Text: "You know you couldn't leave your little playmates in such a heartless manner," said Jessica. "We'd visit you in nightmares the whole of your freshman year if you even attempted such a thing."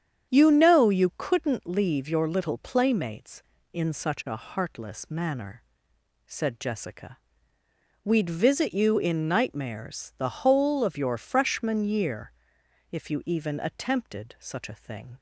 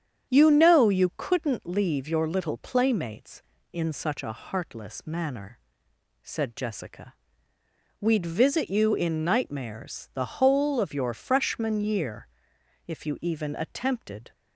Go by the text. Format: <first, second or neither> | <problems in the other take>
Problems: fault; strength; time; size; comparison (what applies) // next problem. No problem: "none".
first | starts louder than the rest; strong; until 1.3 s; 8.5 dB; strong in the first // pauses between "year" and "if"; noticeable; at 12.2 s; 0.58 s long; noticeable in the first // stops before "such a thing"; at 14.3 s